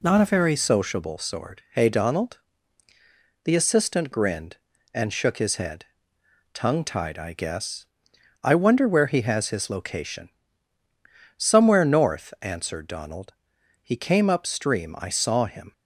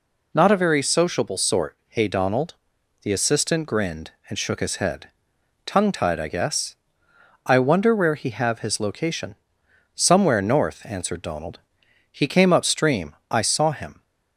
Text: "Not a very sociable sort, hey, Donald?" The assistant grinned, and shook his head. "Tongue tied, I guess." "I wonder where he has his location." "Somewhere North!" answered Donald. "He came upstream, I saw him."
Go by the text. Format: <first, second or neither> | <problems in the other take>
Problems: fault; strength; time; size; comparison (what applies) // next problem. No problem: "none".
first | says "have" for "has"; at 8.3 s